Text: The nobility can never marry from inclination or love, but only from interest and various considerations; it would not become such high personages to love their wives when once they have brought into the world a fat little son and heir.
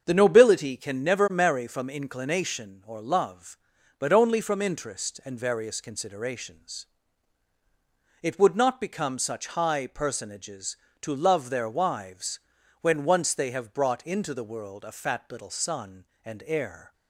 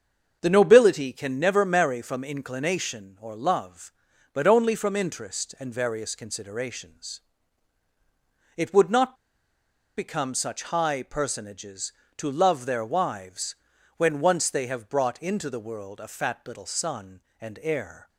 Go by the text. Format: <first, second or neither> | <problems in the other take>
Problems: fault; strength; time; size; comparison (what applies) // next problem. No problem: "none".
first | starts louder than the rest; until 1.4 s; 7 dB; also in the first // pauses between "not" and "become"; noticeable; at 9.1 s; 0.82 s long // pauses between "wives" and "when"; at 13.5 s; 0.40 s long; also in the first